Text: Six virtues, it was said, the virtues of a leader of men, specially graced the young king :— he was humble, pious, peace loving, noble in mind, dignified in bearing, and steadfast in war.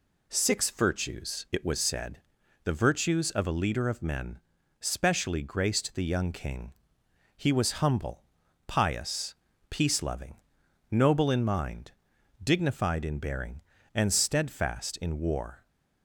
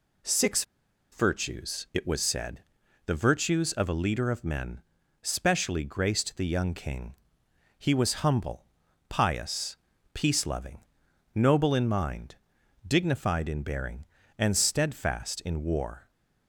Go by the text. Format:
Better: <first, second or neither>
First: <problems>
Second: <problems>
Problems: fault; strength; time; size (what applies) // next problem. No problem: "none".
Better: first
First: none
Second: pauses between "Six" and "virtues"; noticeable; at 0.6 s; 0.49 s long